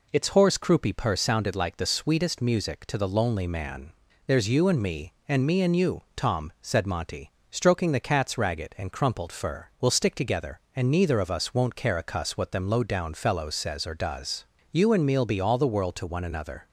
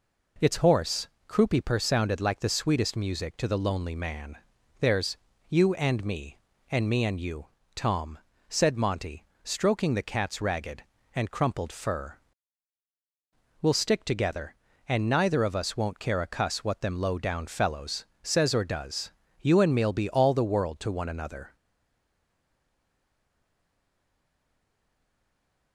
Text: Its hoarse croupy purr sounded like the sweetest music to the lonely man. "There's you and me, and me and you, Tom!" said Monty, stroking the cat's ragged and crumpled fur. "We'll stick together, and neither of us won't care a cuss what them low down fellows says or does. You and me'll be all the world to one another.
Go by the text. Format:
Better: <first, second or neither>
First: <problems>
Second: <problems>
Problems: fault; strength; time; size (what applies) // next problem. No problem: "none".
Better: first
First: none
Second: pauses between "hoarse" and "croupy"; slight; at 1.0 s; 0.20 s long // pauses between "There's" and "you"; slight; at 5.1 s; 0.32 s long // pauses between "fellows" and "says"; slight; at 18.0 s; 0.16 s long // stays silent after the last word; strong; from 21.5 s on; 4.2 s long